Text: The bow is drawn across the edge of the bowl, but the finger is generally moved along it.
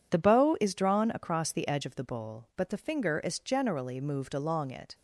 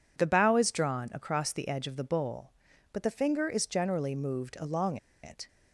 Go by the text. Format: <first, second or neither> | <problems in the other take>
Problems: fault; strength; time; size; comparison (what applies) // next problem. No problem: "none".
first | pauses between "along" and "it"; slight; at 4.9 s; 0.26 s long